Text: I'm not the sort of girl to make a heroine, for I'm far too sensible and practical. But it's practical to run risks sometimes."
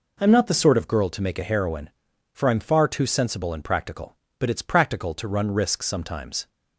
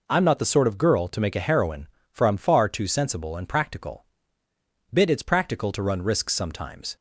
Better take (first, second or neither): first